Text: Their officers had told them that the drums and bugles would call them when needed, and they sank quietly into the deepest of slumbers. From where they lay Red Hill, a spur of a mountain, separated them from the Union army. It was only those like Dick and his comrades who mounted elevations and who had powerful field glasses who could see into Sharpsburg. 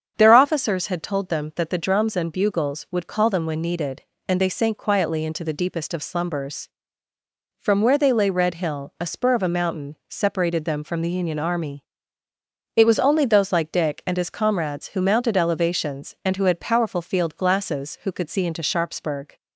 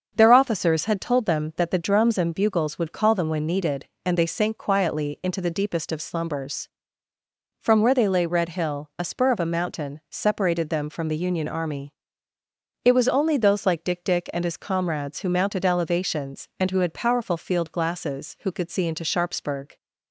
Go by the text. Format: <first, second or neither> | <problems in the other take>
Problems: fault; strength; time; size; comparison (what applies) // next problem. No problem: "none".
first | starts louder than the rest; until 1.1 s; 6.5 dB; strong in the first // says "Dick" twice; at 14.0 s